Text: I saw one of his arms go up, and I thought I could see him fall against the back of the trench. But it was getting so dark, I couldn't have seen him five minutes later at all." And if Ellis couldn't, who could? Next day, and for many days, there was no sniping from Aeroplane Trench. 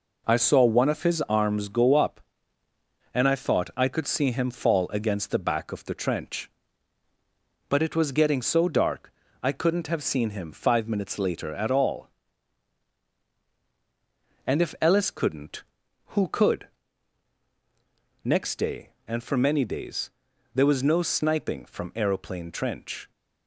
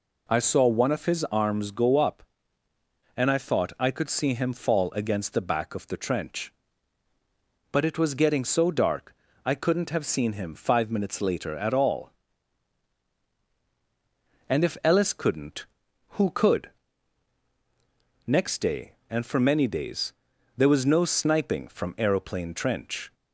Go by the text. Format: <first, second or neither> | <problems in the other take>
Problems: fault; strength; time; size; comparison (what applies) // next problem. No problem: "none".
second | gets quieter; noticeable; throughout; 5.5 dB